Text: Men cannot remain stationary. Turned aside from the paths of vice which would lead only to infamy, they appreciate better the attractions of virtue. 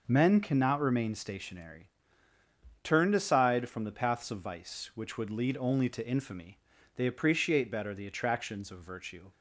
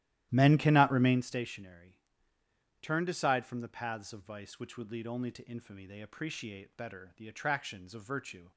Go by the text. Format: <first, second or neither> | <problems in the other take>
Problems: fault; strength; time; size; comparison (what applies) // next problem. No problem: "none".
first | starts louder than the rest; strong; until 1.3 s; 13.5 dB